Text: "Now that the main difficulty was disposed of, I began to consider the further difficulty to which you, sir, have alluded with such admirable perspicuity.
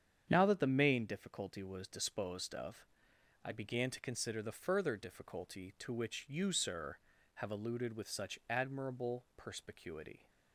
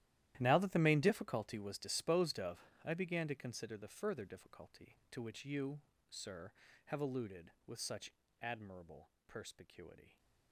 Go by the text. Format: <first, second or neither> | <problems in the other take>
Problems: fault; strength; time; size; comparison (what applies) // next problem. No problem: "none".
first | gets quieter; strong; throughout; 15.5 dB // starts louder than the rest; strong; until 1.3 s; 13 dB; strong in the first // pauses between "such" and "admirable"; slight; at 8.1 s; 0.30 s long // pauses between "admirable" and "perspicuity"; slight; at 9.0 s; 0.18 s long